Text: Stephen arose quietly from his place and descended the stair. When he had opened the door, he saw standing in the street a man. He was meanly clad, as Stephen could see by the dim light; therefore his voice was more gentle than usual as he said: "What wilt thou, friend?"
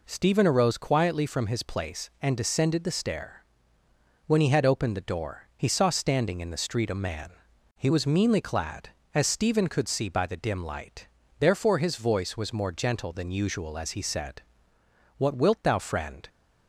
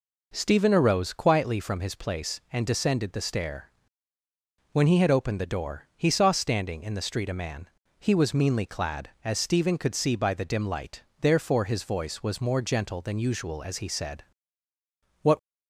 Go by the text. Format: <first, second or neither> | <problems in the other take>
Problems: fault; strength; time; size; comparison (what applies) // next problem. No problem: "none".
first | stops before "wilt thou friend"; at 15.3 s